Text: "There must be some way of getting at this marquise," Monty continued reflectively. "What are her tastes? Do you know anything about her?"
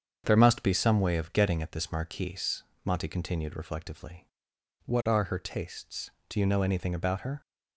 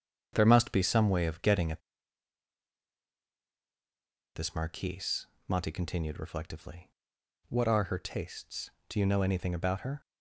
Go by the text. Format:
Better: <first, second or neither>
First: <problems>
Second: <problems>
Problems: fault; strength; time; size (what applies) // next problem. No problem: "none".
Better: first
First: starts louder than the rest; strong; until 1.2 s; 7.5 dB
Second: starts louder than the rest; strong; until 1.3 s; 7 dB // pauses between "at" and "this"; strong; at 1.8 s; 2.5 s long